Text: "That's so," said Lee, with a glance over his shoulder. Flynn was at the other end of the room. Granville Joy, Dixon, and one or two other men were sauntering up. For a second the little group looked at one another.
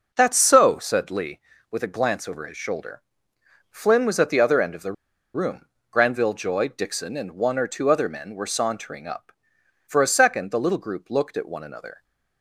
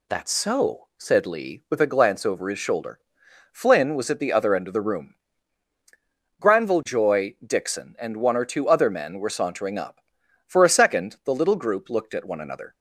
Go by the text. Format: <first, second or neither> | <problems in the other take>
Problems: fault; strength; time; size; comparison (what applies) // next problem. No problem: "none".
second | pauses between "the" and "room"; at 4.9 s; 0.42 s long